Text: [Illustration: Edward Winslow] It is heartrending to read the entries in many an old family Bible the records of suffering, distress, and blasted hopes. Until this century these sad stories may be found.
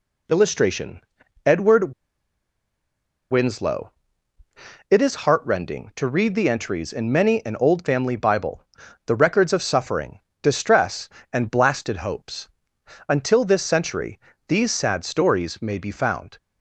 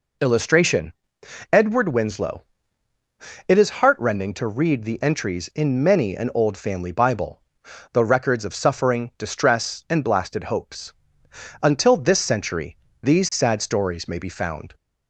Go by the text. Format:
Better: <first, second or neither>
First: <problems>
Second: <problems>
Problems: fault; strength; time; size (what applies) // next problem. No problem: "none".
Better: second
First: pauses between "Edward" and "Winslow"; strong; at 1.9 s; 1.3 s long // pauses between "Winslow" and "It"; noticeable; at 3.9 s; 0.98 s long // pauses between "Bible" and "the"; at 8.6 s; 0.40 s long // pauses between "century" and "these"; slight; at 14.1 s; 0.30 s long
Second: pauses between "Winslow" and "It"; at 2.4 s; 1.0 s long // pauses between "Bible" and "the"; noticeable; at 7.4 s; 0.50 s long // pauses between "century" and "these"; slight; at 12.7 s; 0.24 s long